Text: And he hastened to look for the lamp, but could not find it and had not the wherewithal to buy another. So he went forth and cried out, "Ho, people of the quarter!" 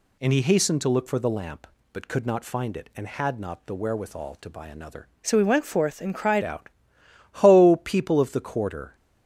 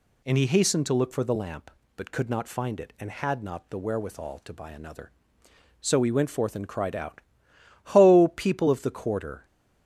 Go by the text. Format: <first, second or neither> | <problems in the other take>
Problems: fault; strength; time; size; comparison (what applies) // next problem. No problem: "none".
second | changes voice from "So" to "cried"; from 5.2 to 6.4 s; 1.2 s long